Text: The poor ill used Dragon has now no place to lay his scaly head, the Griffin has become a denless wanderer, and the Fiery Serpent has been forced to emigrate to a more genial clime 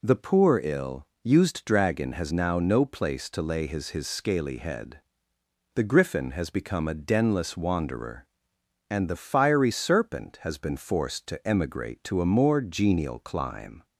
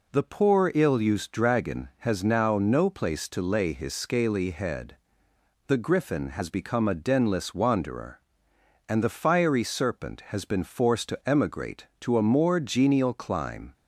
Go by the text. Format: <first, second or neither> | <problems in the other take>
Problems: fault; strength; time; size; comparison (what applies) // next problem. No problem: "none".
second | pauses between "ill" and "used"; slight; at 1.0 s; 0.16 s long // says "his" twice; at 3.9 s